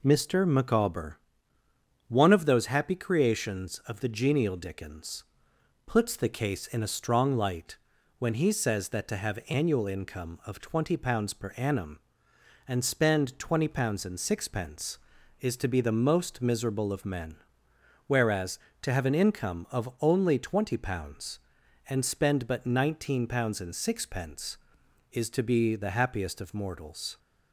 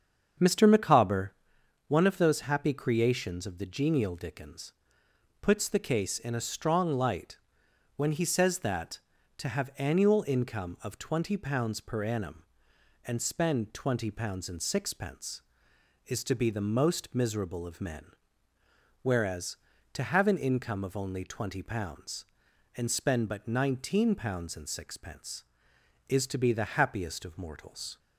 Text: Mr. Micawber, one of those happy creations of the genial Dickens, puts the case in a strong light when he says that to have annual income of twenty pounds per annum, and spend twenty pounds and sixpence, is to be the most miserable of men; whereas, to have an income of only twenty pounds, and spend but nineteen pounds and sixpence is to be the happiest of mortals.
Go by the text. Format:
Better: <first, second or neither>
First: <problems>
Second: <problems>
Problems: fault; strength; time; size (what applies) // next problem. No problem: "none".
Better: first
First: pauses between "light" and "when"; at 7.7 s; 0.42 s long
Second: starts louder than the rest; strong; until 1.6 s; 7.5 dB // pauses between "light" and "when"; noticeable; at 7.3 s; 0.58 s long